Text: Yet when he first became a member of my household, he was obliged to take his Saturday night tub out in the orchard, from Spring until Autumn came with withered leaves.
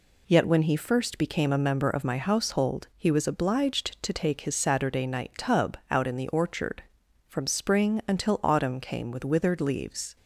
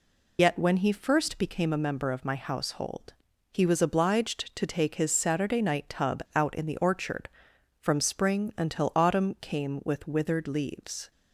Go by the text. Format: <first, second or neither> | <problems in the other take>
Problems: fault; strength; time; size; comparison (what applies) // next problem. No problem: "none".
first | loses the start of "Yet"; at 0.3 s; 60 ms